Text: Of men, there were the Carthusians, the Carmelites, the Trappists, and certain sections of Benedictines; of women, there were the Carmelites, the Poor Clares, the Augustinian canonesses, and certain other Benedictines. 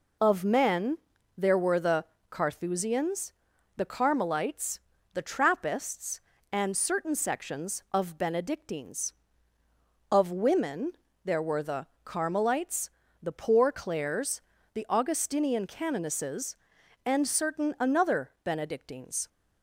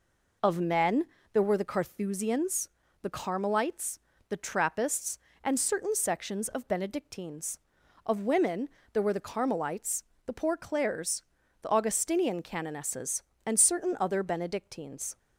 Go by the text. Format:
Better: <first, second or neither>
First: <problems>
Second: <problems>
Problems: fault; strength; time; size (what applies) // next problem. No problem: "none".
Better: second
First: pauses between "the" and "Carthusians"; slight; at 2.0 s; 0.26 s long // pauses between "the" and "Carmelites"; slight; at 11.8 s; 0.18 s long // says "another" for "other"; at 17.7 s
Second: none